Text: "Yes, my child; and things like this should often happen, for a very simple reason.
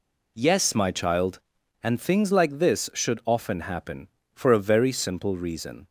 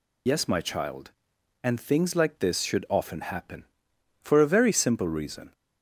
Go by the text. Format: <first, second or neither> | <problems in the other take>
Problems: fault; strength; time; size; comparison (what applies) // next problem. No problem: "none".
first | loses the start of "Yes"; at 0.2 s; 75 ms